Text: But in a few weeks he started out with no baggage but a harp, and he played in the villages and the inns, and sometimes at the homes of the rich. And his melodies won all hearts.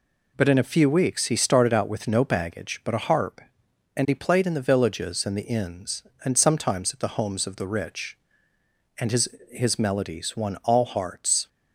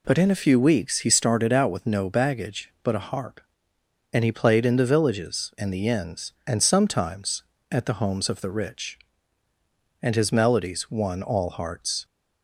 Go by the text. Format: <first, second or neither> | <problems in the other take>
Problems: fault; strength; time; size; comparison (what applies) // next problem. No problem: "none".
second | says "his" twice; at 9.4 s